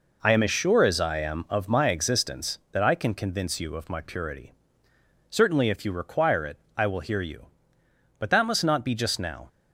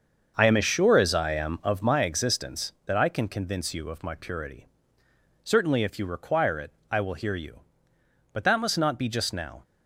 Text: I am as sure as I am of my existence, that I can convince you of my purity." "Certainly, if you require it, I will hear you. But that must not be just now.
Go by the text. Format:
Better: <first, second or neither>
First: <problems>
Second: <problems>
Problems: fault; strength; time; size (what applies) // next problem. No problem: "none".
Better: first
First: none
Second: starts louder than the rest; until 2.0 s; 6.5 dB